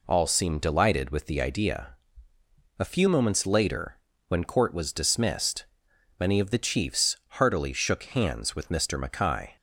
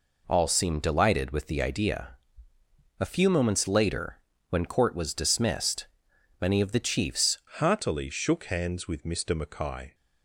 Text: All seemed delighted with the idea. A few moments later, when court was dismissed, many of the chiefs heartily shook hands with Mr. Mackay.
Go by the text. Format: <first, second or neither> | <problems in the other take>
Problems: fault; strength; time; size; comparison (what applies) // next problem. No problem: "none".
first | changes voice at "heartily"; from 7.5 s on; 2.4 s long